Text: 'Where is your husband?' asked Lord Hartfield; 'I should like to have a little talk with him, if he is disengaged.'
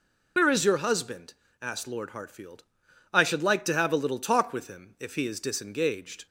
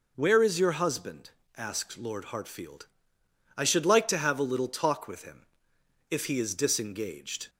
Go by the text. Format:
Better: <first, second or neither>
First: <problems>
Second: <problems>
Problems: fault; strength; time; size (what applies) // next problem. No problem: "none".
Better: second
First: loses the start of "Where"; at 0.3 s; 65 ms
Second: none